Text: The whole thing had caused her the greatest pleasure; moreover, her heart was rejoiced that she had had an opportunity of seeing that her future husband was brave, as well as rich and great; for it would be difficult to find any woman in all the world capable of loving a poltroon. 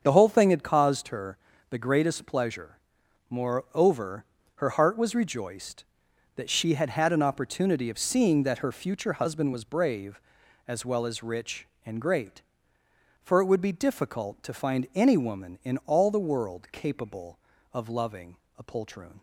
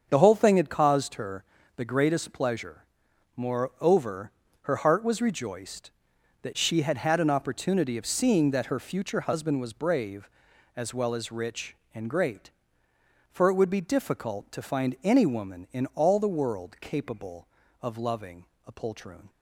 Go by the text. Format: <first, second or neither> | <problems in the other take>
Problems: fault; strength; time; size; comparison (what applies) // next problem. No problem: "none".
neither | starts louder than the rest; strong; the same in both // pauses between "her" and "the"; slight; the same in both // pauses between "loving" and "a"; slight; the same in both